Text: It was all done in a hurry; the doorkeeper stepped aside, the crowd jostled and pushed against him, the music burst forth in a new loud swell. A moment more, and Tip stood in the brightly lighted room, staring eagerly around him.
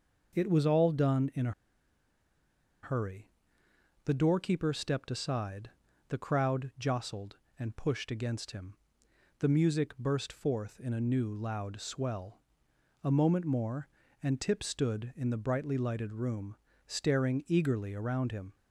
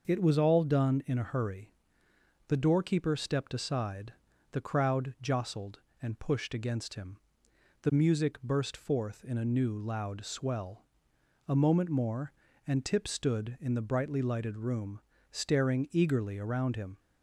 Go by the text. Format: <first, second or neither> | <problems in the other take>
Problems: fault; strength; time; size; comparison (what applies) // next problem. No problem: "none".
second | starts louder than the rest; noticeable; until 1.4 s; 6 dB; noticeable in the second // pauses between "a" and "hurry"; strong; at 1.5 s; 1.3 s long